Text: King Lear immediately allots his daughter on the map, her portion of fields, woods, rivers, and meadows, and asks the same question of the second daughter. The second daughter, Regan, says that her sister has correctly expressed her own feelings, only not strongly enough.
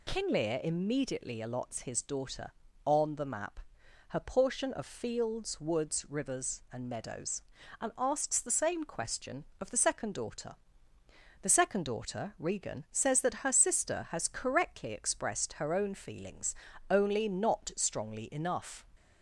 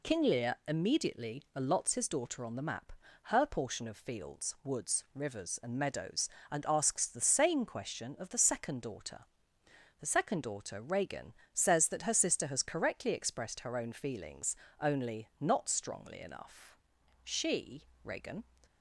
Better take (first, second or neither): first